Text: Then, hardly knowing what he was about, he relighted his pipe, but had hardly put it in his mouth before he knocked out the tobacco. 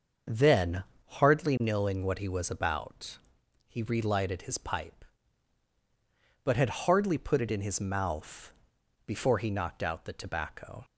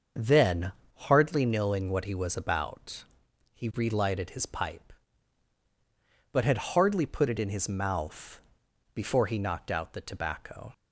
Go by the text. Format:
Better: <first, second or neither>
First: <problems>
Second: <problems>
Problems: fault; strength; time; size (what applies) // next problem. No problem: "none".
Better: neither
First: starts louder than the rest; until 1.5 s; 6.5 dB // pauses between "mouth" and "before"; noticeable; at 8.5 s; 0.54 s long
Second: starts louder than the rest; until 1.4 s; 6.5 dB // pauses between "mouth" and "before"; noticeable; at 8.4 s; 0.54 s long